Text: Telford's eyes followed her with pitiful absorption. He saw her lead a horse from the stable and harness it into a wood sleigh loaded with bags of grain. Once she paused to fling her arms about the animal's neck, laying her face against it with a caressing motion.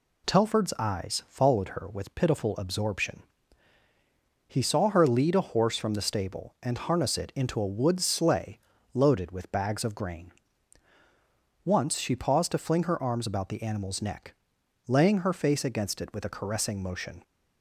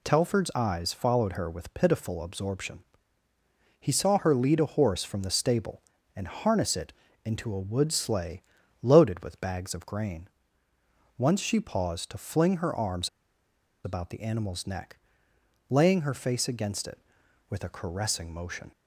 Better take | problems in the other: first | pauses between "it" and "into"; slight; at 6.9 s; 0.32 s long // pauses between "sleigh" and "loaded"; at 8.4 s; 0.40 s long; slight in the first // pauses between "arms" and "about"; noticeable; at 13.0 s; 0.76 s long

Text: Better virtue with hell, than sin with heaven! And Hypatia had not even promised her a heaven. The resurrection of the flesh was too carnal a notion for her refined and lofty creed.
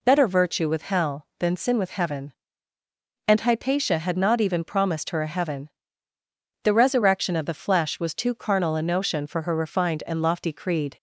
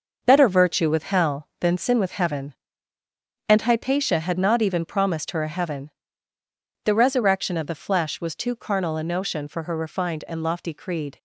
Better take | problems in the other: first | gets quieter; throughout; 6.5 dB

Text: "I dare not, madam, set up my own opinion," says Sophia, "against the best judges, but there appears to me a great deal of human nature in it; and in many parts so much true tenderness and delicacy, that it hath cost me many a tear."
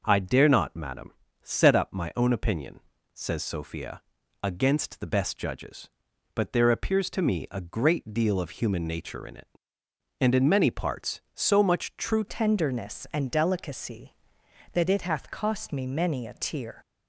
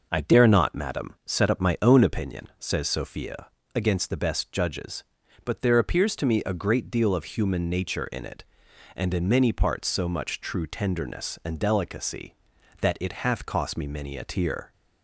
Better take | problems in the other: second | changes voice at "tenderness"; from 12.2 s on; 4.6 s long

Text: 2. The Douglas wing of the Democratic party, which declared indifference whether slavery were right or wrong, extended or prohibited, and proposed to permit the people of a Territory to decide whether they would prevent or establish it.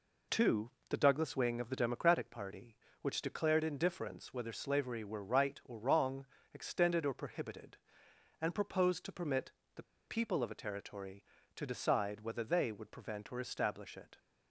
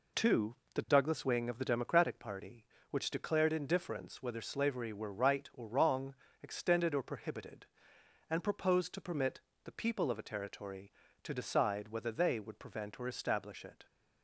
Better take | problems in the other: second | pauses between "permit" and "the"; slight; at 9.5 s; 0.24 s long; slight in the second // pauses between "the" and "people"; slight; at 9.8 s; 0.23 s long

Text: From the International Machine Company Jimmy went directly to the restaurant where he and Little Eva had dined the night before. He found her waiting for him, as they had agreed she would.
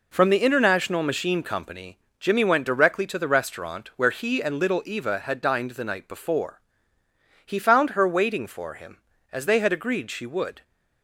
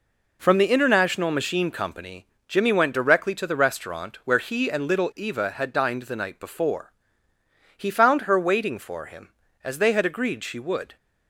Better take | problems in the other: neither | pauses between "Company" and "Jimmy"; slight; the same in both

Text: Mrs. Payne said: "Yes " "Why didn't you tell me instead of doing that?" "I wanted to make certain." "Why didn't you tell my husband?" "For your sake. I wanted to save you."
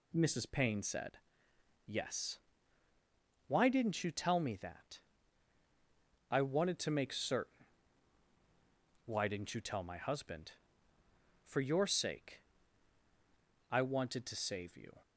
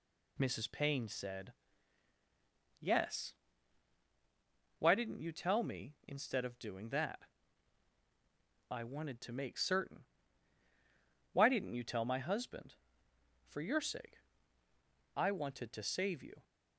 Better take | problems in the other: second | skips "instead of doing"; at 4.5 s

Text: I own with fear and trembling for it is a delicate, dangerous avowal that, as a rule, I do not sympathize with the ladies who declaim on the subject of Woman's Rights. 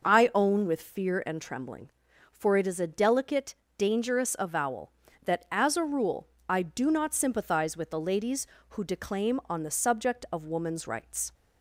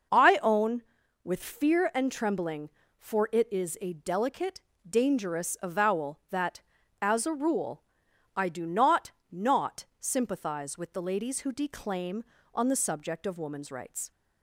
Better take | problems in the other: first | says "not" twice; at 9.3 s

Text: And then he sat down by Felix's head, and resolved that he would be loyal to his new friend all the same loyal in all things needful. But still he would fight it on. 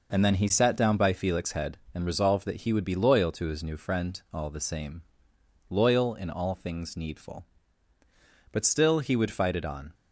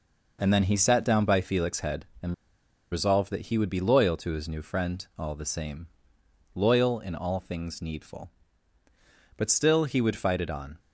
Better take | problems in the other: first | pauses between "and" and "resolved"; noticeable; at 2.3 s; 0.57 s long // pauses between "same" and "loyal"; noticeable; at 5.8 s; 0.68 s long; noticeable in the first

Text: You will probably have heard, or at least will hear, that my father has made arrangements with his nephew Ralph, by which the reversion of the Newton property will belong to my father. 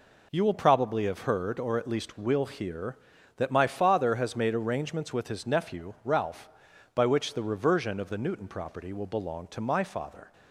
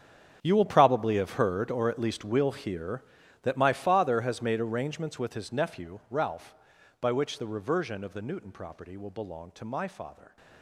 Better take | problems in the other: first | gets quieter; strong; throughout; 16 dB

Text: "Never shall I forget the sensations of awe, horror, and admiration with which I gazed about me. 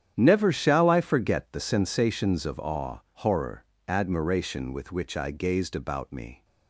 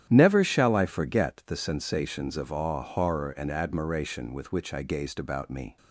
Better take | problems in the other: second | starts louder than the rest; strong; until 1.1 s; 9.5 dB; strong in the second // skips "and"; at 3.7 s

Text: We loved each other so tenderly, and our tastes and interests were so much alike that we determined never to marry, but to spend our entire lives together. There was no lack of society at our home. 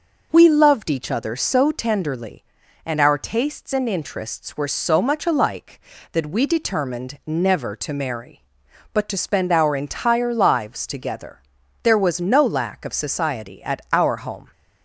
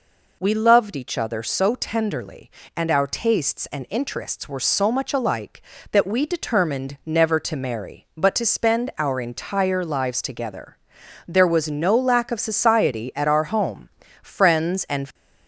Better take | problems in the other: first | goes on to say "Friends and"; noticeable; from 14.2 s on; 0.90 s long

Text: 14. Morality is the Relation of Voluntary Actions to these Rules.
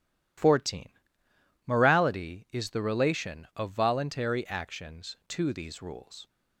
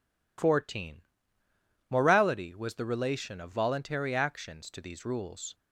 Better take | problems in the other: first | says "was" for "is"; at 2.5 s

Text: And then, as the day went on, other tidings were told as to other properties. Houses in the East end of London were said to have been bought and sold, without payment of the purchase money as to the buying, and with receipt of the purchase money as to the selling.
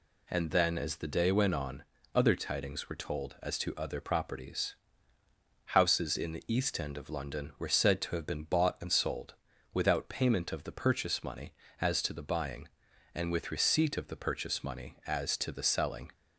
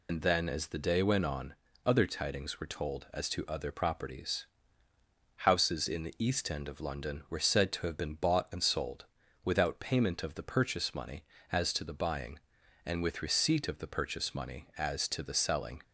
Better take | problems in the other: first | loses the start of "And"; at 0.0 s; 100 ms

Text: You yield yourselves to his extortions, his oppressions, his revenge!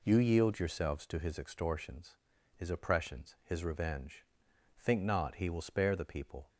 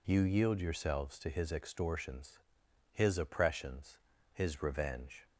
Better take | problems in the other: second | goes on to say "Think not he will spare the people"; strong; from 4.8 s on; 1.6 s long

